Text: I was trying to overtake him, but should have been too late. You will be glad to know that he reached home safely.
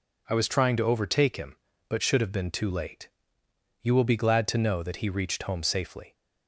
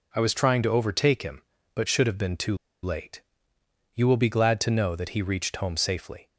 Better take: first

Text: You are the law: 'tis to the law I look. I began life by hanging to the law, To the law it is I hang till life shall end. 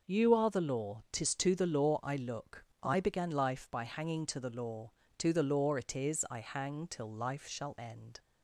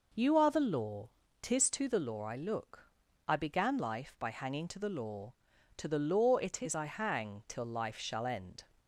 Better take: neither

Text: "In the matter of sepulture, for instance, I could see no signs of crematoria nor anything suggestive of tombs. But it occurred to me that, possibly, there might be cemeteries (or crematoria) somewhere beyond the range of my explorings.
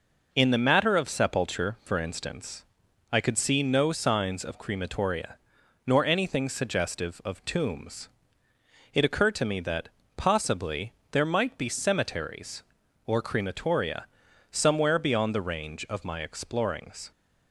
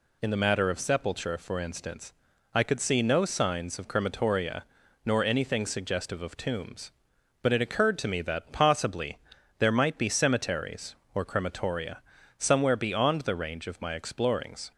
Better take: second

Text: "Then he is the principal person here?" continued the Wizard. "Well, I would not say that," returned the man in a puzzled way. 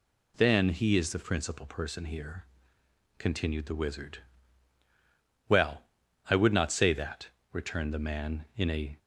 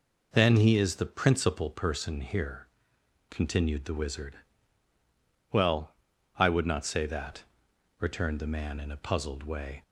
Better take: second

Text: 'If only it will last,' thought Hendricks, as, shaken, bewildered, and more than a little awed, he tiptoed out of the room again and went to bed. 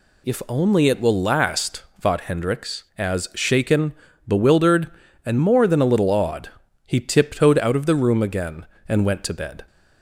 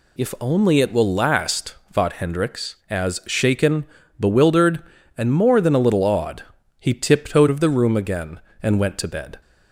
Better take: first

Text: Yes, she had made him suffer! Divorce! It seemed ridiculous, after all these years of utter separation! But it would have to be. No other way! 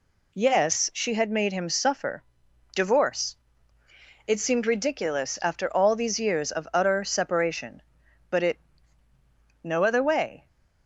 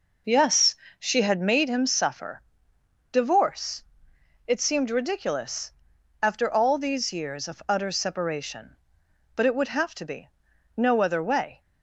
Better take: second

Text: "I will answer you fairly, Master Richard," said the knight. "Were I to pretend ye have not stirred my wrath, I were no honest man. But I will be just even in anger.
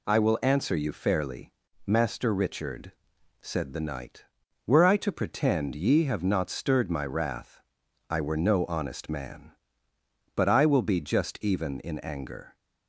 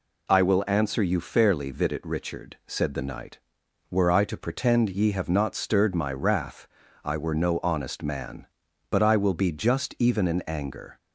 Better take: first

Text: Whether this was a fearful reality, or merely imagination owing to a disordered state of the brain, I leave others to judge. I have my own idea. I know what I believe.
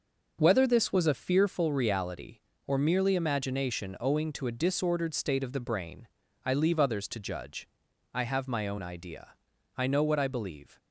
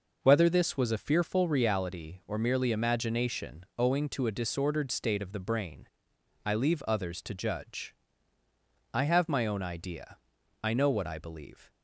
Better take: neither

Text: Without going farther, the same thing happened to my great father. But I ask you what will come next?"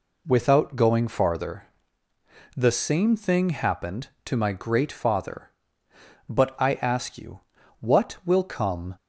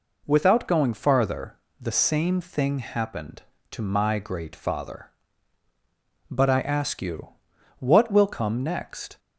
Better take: second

